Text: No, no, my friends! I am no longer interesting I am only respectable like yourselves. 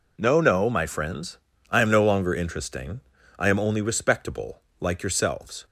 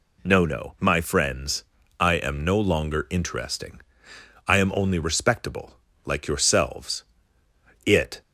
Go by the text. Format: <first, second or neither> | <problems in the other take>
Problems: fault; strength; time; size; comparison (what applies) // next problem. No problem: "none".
first | pauses between "interesting" and "I"; noticeable; at 3.8 s; 0.66 s long; also in the first // pauses between "respectable" and "like"; slight; at 5.7 s; 0.34 s long; slight in the first // goes on to say "It"; slight; from 7.8 s on; 0.36 s long